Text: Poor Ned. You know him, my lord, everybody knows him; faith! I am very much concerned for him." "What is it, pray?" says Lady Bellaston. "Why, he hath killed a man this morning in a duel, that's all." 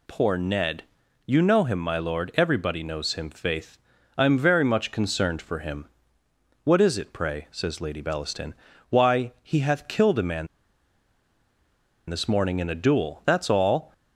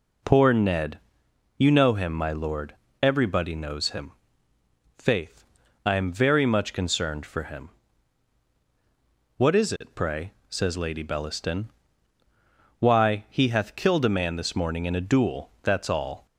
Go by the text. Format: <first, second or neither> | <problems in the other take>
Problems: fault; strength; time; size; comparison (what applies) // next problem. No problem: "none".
second | pauses between "man" and "this"; strong; at 10.4 s; 1.6 s long